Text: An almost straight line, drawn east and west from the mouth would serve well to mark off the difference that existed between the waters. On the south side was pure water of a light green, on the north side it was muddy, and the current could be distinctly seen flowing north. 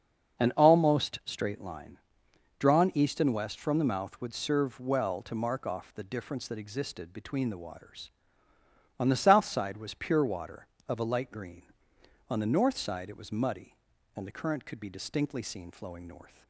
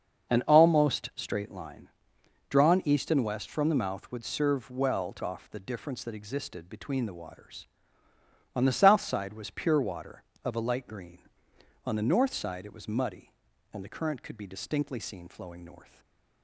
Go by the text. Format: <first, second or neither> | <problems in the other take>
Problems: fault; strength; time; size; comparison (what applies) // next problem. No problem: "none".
first | starts louder than the rest; until 1.4 s; 6.5 dB; also in the first // skips "mark"; at 5.2 s // stays silent after the last word; slight; from 15.8 s on; 0.6 s long